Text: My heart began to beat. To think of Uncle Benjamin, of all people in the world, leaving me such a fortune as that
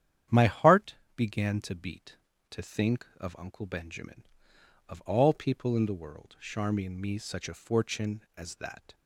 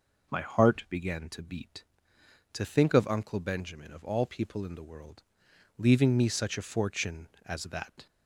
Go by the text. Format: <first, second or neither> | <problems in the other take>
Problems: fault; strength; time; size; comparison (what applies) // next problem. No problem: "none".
second | starts louder than the rest; strong; until 1.4 s; 10 dB // pauses between "heart" and "began"; slight; at 0.9 s; 0.20 s long // says "charmian" for "leaving"; at 6.4 s